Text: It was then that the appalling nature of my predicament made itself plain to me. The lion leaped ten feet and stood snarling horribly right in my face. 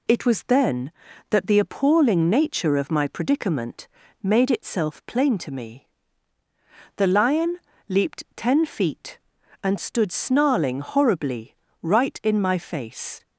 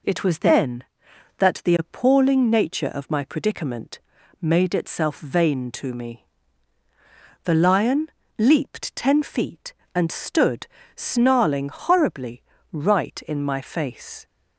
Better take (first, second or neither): first